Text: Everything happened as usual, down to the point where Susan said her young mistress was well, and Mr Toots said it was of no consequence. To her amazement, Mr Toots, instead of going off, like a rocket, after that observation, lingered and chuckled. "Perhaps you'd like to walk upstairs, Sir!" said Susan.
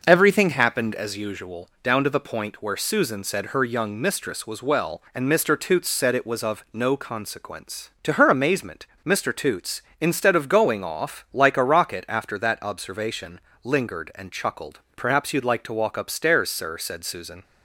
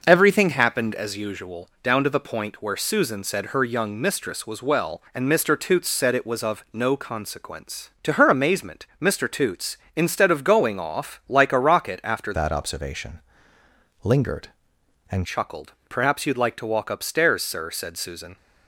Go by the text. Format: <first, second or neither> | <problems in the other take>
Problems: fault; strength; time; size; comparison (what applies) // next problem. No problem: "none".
first | changes voice from "that" to "and"; from 12.3 to 15.2 s; 2.9 s long